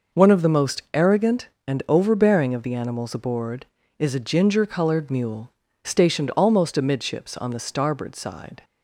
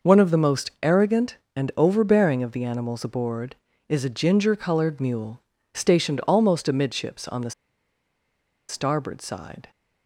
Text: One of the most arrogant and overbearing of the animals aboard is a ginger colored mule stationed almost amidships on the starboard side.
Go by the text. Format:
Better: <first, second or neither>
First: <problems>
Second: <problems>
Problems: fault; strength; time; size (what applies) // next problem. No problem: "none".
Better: first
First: pauses between "mule" and "stationed"; slight; at 5.5 s; 0.32 s long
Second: pauses between "mule" and "stationed"; slight; at 5.4 s; 0.32 s long // pauses between "the" and "starboard"; at 7.5 s; 1.1 s long